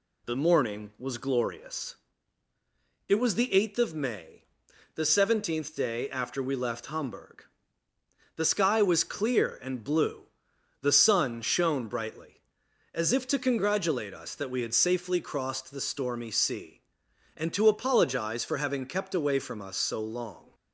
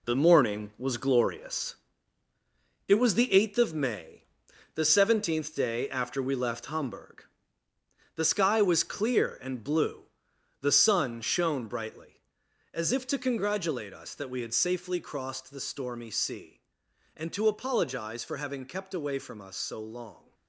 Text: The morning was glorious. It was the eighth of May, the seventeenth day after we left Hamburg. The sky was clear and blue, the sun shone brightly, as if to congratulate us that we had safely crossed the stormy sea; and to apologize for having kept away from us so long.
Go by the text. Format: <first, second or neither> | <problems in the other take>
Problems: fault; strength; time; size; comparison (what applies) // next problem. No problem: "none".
first | gets quieter; strong; throughout; 7.5 dB